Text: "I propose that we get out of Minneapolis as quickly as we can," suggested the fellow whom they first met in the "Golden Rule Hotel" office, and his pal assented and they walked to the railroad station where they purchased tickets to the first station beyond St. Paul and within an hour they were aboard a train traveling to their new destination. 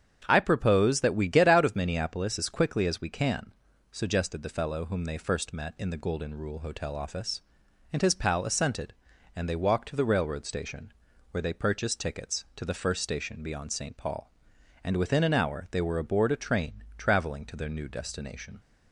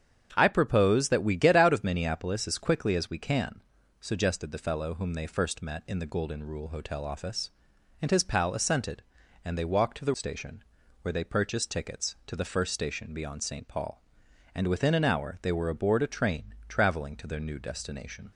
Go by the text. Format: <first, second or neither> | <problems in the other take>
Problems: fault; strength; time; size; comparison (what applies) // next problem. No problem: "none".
first | starts louder than the rest; strong; until 1.3 s; 8 dB; strong in the first // skips "railroad"; at 10.1 s // pauses between "station" and "where"; at 10.6 s; 0.38 s long; also in the first